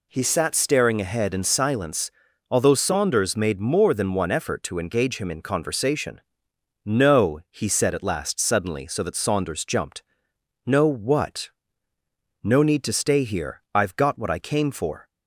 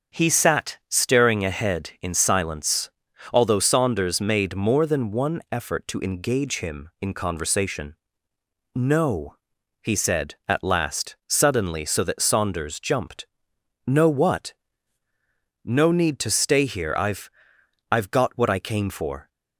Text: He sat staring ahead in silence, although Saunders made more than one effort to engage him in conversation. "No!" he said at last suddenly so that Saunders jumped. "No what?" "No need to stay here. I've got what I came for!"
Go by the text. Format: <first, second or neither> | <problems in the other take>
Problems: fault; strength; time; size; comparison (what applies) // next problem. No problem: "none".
first | starts louder than the rest; until 1.2 s; 6.5 dB // says "I've" twice; at 17.9 s